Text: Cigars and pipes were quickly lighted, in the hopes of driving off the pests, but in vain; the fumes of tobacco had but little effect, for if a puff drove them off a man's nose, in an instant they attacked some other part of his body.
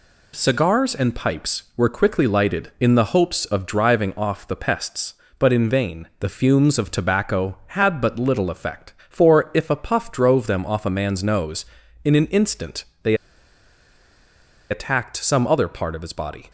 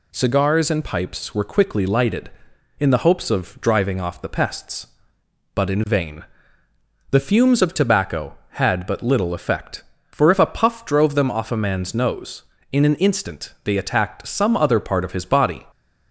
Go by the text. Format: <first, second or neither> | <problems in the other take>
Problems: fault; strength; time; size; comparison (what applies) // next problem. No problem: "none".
second | pauses between "instant" and "they"; slight; at 12.8 s; 0.22 s long // pauses between "they" and "attacked"; strong; at 13.1 s; 1.5 s long